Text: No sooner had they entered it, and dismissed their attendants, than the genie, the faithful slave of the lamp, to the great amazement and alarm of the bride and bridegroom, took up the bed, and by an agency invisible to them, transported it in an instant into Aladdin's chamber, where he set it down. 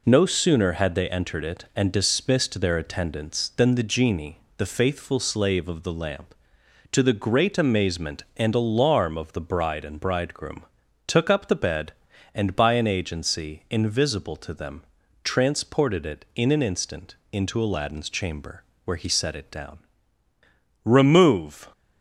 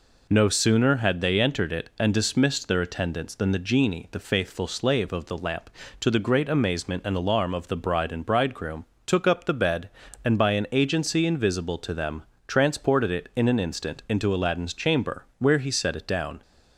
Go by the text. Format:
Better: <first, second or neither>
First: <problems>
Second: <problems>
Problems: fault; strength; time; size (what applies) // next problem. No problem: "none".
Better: second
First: pauses between "instant" and "into"; slight; at 17.1 s; 0.18 s long // goes on to say "Remove"; noticeable; from 20.8 s on; 0.88 s long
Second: none